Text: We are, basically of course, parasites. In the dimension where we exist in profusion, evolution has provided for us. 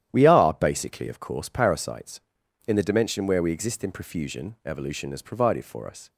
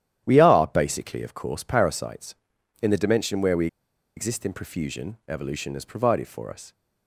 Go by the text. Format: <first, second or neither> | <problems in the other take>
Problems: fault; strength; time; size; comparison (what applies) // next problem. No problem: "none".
first | starts louder than the rest; strong; until 1.2 s; 11 dB; strong in the first // pauses between "we" and "exist"; noticeable; at 3.6 s; 0.49 s long